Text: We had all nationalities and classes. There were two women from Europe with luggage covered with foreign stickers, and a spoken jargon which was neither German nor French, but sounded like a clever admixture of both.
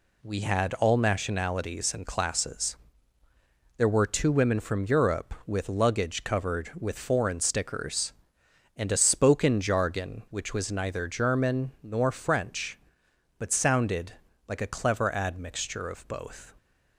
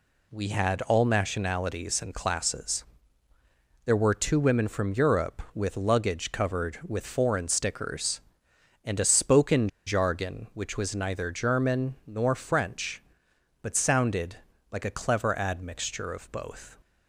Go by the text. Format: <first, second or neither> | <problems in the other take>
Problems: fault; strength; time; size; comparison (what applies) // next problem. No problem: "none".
first | pauses between "spoken" and "jargon"; slight; at 9.6 s; 0.17 s long // pauses between "sounded" and "like"; slight; at 14.3 s; 0.34 s long; slight in the first